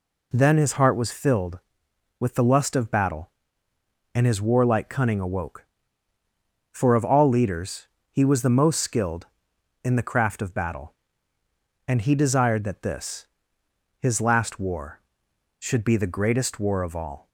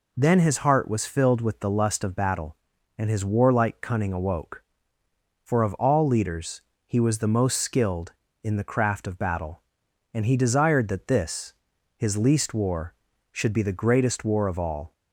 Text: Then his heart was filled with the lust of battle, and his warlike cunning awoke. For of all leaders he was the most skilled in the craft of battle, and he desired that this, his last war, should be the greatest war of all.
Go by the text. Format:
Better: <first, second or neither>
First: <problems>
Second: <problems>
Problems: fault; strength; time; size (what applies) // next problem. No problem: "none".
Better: first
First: pauses between "leaders" and "he"; slight; at 7.8 s; 0.24 s long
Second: pauses between "leaders" and "he"; slight; at 6.6 s; 0.24 s long // says "least" for "last"; at 12.1 s